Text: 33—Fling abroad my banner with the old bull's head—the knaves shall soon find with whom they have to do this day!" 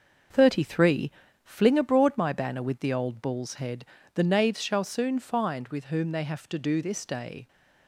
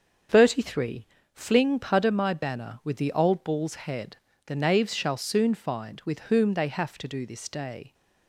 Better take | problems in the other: first | starts louder than the rest; until 1.5 s; 7 dB // says "pudder" for "abroad"; at 1.8 s

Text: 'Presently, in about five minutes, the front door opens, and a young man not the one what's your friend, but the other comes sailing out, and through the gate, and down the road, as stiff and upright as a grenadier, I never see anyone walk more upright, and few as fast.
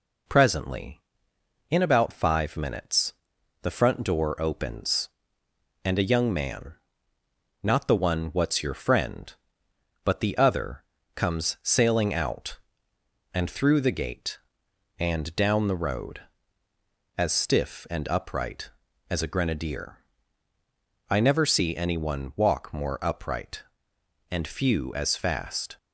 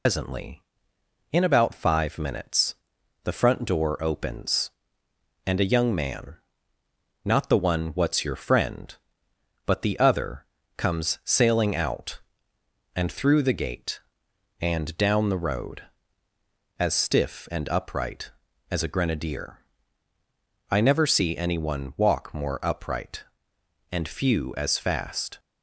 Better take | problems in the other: first | loses the start of "Presently"; at 0.0 s; 150 ms // pauses between "man" and "not"; noticeable; at 6.3 s; 0.88 s long; noticeable in the first // pauses between "other" and "comes"; slight; at 10.4 s; 0.32 s long; slight in the first

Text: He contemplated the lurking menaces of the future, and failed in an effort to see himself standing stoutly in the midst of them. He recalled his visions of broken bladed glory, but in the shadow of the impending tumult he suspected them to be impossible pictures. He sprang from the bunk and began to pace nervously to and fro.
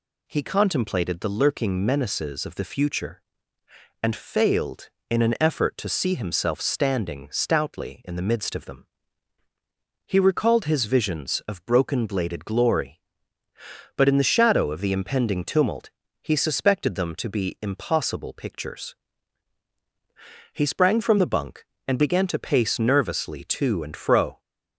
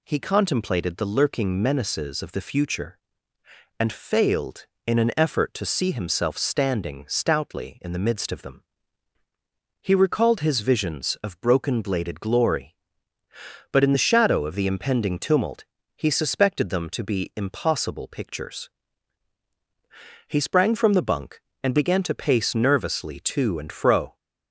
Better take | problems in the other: neither | pauses between "tumult" and "he"; slight; the same in both

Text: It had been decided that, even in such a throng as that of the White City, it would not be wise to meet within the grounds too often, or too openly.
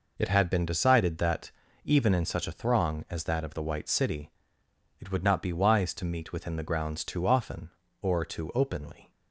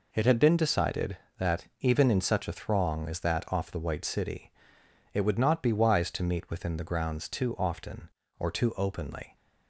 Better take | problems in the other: first | says "off" for "of"; at 3.5 s

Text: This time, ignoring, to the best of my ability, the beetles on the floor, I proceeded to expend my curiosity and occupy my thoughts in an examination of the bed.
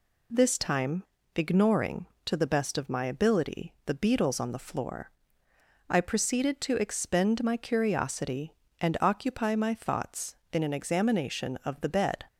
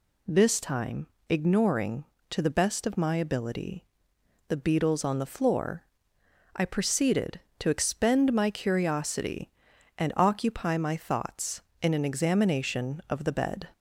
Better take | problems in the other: neither | none

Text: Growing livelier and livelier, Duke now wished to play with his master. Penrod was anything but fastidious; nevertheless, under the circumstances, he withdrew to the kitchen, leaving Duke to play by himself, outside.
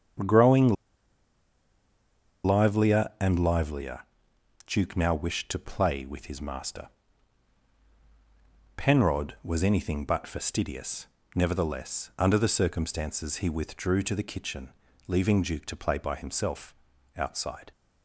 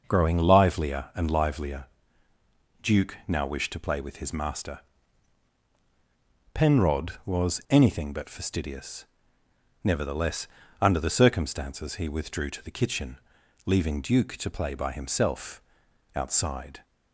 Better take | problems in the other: second | starts louder than the rest; strong; until 2.9 s; 7.5 dB; noticeable in the second // pauses between "Growing" and "livelier"; strong; at 0.7 s; 1.7 s long

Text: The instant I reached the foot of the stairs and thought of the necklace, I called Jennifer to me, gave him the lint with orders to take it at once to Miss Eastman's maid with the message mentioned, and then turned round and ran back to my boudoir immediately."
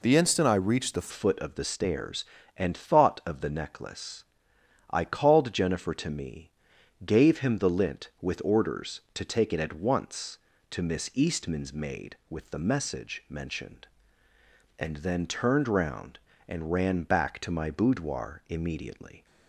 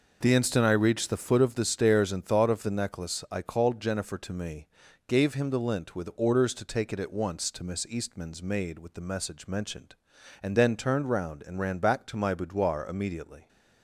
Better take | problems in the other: second | changes voice at "foot"; from 1.0 s on; 18.2 s long

